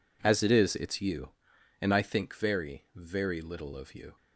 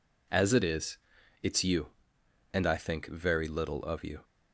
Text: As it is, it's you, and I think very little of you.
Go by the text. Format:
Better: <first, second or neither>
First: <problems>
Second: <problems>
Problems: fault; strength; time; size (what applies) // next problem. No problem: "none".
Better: second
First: says "very" twice; at 2.9 s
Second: none